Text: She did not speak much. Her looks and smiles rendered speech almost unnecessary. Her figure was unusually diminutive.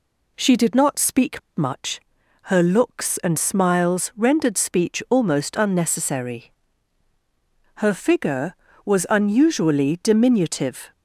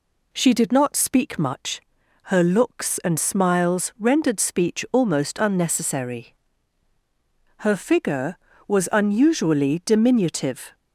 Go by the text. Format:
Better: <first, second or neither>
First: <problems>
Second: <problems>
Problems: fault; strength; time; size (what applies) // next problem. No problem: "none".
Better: second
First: pauses between "speak" and "much"; slight; at 1.3 s; 0.17 s long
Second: none